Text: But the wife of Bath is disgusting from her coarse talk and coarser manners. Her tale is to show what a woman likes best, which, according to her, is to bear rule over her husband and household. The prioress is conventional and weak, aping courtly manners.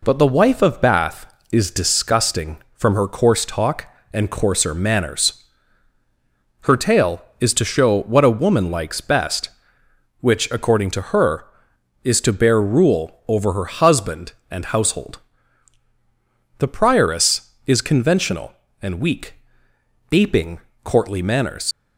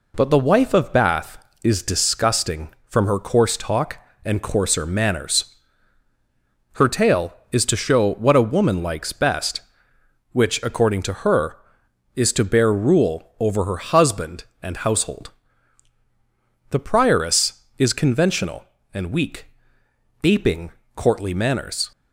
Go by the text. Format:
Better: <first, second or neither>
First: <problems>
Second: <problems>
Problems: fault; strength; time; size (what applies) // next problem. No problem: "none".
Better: second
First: pauses between "aping" and "courtly"; slight; at 20.5 s; 0.24 s long // leaves "manners" unfinished; at 21.7 s; 85 ms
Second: pauses between "aping" and "courtly"; slight; at 20.7 s; 0.24 s long